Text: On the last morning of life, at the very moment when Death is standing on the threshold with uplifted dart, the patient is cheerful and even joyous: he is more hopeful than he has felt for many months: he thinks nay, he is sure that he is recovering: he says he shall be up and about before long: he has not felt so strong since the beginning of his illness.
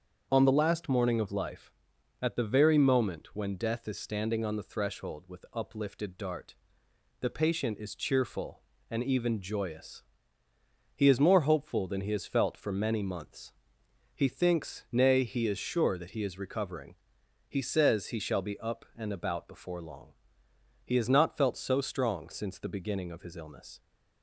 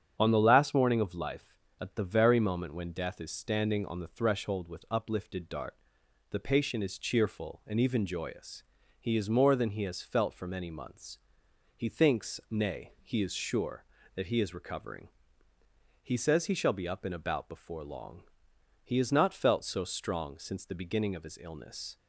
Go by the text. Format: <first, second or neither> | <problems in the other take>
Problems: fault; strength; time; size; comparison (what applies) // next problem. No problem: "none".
first | starts louder than the rest; strong; until 1.2 s; 8 dB; also in the first // skips "hopeful"; at 9.5 s